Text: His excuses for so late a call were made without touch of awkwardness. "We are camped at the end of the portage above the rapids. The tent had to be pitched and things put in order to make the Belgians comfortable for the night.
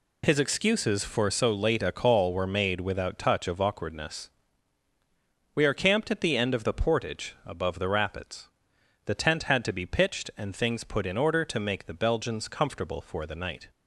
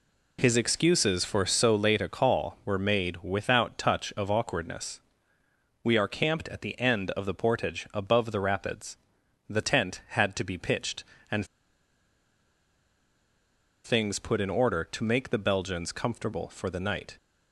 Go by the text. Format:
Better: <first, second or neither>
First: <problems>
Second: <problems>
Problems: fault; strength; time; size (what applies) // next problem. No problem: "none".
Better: first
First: none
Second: pauses between "and" and "things"; strong; at 11.4 s; 2.3 s long